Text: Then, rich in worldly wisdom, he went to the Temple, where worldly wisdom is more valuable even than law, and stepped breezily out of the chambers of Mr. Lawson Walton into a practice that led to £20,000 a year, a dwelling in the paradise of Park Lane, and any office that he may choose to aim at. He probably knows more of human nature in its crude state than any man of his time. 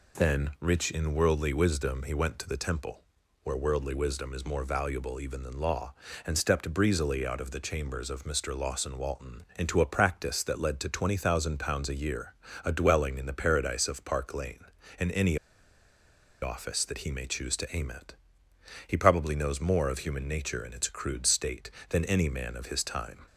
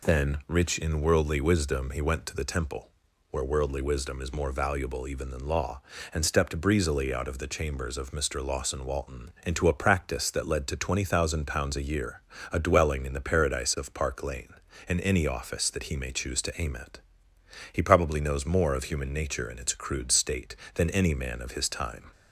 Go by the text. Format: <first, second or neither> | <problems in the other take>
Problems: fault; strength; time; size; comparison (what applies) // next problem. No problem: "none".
second | pauses between "any" and "office"; at 15.3 s; 1.0 s long